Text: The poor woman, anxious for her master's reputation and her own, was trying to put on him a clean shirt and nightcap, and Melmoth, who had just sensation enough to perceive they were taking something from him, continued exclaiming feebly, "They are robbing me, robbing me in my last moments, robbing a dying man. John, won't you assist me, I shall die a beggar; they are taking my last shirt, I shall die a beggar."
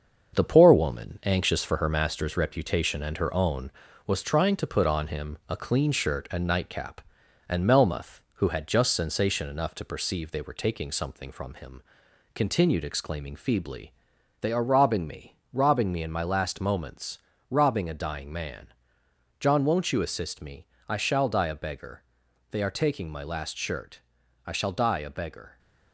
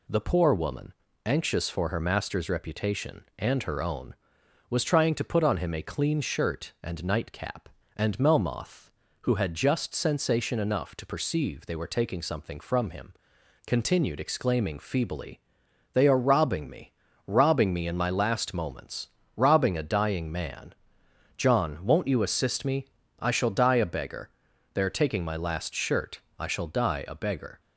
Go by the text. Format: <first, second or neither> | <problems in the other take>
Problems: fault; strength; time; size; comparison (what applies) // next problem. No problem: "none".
second | gets quieter; noticeable; throughout; 5 dB